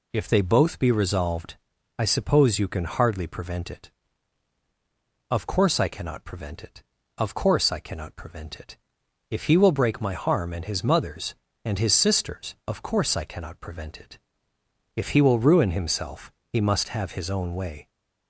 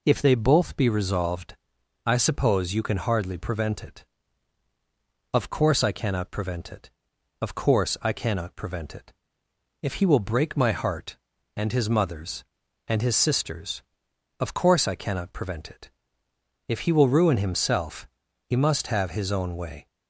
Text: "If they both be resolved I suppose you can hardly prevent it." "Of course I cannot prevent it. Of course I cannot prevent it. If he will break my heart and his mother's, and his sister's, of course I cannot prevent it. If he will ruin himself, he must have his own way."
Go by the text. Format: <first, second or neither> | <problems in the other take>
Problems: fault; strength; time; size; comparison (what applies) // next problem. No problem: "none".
second | pauses between "resolved" and "I"; at 1.5 s; 0.42 s long; noticeable in the second // says "harm" for "heart"; at 10.1 s